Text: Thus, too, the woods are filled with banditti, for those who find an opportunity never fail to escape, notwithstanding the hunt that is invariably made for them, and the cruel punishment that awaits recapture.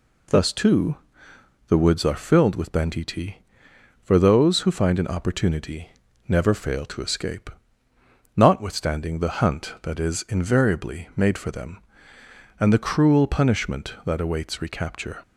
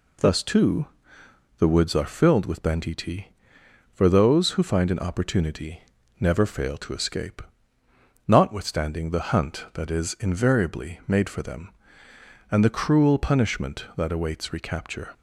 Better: neither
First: pauses between "opportunity" and "never"; at 5.8 s; 0.38 s long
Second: pauses between "opportunity" and "never"; at 5.8 s; 0.38 s long

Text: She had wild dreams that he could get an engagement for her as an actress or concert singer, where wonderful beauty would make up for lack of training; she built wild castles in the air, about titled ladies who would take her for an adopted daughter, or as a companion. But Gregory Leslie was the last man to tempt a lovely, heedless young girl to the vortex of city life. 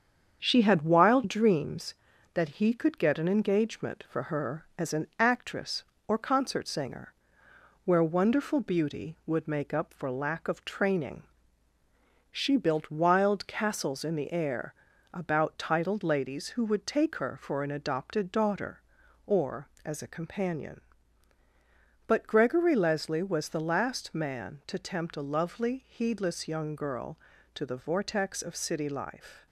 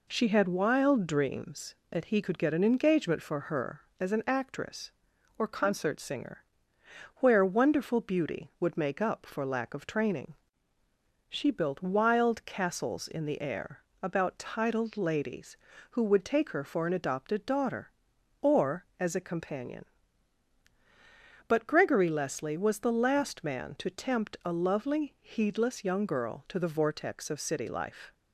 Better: second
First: gets quieter; noticeable; throughout; 4 dB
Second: none

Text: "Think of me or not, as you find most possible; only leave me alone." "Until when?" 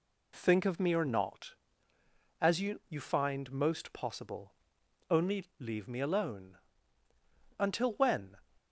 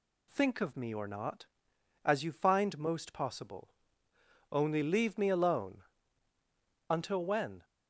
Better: second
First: says "you" twice; at 2.8 s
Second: none

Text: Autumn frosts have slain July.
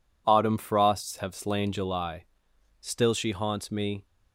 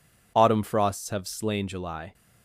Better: second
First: goes on to say "Still she haunts me"; noticeable; from 2.8 s on; 1.2 s long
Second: none

